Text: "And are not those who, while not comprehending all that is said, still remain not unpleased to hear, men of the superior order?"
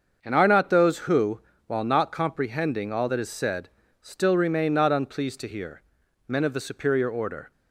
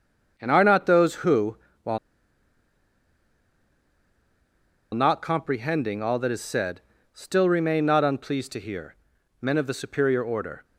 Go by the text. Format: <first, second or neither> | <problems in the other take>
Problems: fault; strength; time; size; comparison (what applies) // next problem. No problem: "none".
first | starts louder than the rest; until 1.3 s; 7 dB; also in the first // pauses between "while" and "not"; strong; at 1.9 s; 2.9 s long